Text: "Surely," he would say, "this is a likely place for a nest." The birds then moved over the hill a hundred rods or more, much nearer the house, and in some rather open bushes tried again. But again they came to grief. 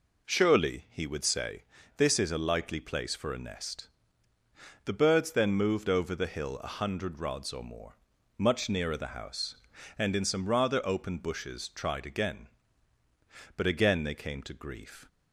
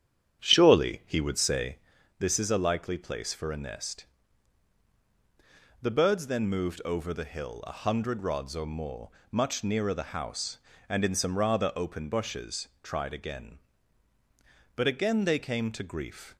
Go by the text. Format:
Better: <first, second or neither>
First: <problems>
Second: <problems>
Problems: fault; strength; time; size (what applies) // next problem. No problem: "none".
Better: first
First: none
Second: starts louder than the rest; strong; until 2.0 s; 9 dB